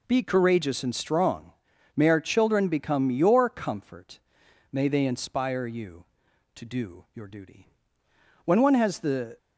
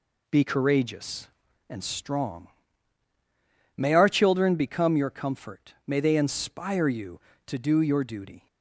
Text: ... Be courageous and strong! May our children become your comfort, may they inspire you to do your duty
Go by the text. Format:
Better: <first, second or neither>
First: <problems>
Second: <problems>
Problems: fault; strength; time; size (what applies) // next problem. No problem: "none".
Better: second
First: goes on to say "When one has the"; noticeable; from 8.4 s on; 0.92 s long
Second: none